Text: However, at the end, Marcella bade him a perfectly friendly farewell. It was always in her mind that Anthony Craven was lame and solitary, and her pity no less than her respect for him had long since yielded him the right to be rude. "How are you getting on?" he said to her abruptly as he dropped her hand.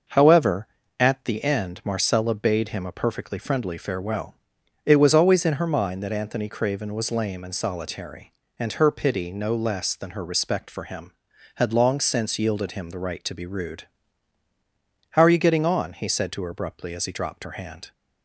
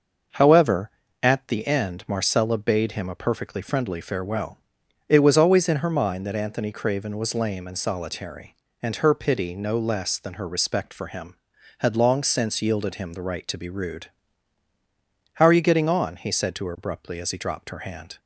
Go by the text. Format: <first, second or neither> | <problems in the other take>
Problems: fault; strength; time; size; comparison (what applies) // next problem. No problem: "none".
neither | none